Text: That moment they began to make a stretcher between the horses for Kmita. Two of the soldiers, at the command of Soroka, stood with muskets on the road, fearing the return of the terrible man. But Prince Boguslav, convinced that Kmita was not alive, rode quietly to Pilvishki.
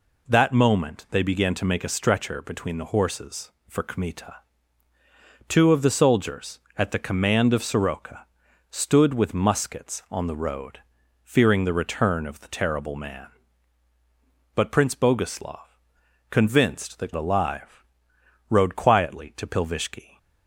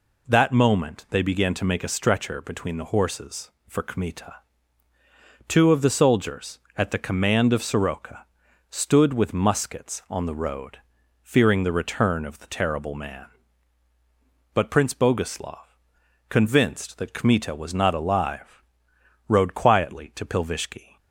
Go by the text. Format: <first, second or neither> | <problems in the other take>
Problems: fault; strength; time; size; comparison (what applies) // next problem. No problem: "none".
second | skips "Kmita was not"; at 17.1 s